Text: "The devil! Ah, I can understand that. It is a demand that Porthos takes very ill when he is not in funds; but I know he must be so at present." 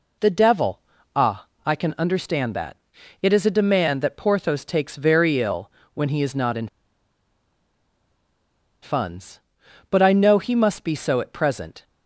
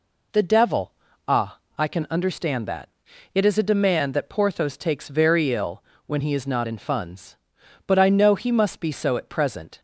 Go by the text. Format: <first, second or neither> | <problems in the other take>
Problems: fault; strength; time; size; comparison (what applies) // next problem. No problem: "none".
second | pauses between "ill" and "when"; slight; at 5.6 s; 0.24 s long; slight in the second // pauses between "in" and "funds"; strong; at 6.6 s; 2.1 s long